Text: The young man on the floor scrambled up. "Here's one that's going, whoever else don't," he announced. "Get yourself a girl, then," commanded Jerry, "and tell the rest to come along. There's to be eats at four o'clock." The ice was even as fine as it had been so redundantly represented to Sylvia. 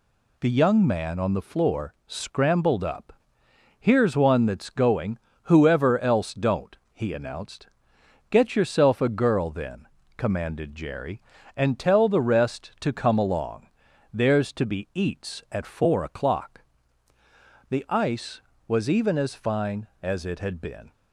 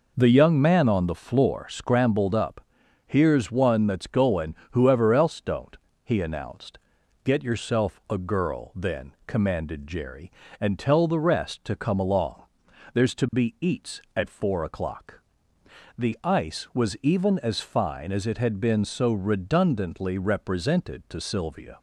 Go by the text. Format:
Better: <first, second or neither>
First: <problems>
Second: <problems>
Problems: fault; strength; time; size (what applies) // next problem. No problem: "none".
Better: second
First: stops before "so redundantly represented to Sylvia"; at 20.9 s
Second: none